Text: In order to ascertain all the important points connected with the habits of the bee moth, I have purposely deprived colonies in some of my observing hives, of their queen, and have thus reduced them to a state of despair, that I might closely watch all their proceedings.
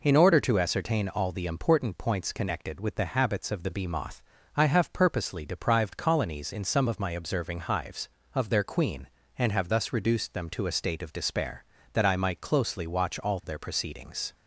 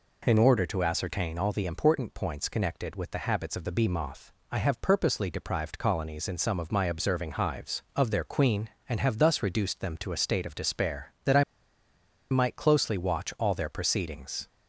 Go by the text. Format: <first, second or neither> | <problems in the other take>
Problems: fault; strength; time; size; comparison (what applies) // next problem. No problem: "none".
first | pauses between "I" and "might"; noticeable; at 11.4 s; 0.87 s long